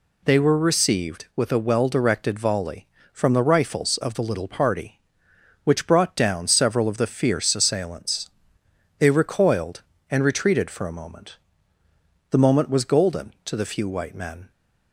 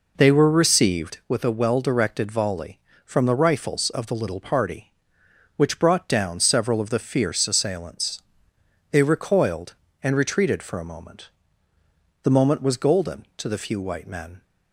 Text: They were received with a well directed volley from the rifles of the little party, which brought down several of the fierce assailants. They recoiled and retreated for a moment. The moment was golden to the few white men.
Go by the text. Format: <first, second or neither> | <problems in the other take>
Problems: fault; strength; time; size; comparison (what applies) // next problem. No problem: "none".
first | starts louder than the rest; noticeable; until 1.3 s; 4.5 dB